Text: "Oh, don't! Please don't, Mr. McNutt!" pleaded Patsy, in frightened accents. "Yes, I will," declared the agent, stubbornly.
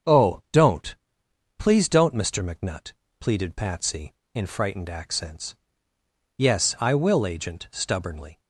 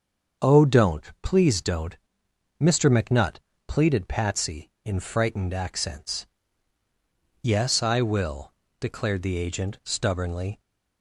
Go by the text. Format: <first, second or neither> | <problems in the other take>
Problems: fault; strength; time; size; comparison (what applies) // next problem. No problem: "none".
second | starts louder than the rest; strong; until 1.8 s; 7 dB; also in the second // skips "declared the"; at 7.2 s